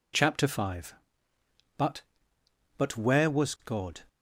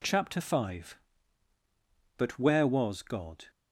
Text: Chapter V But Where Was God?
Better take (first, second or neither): second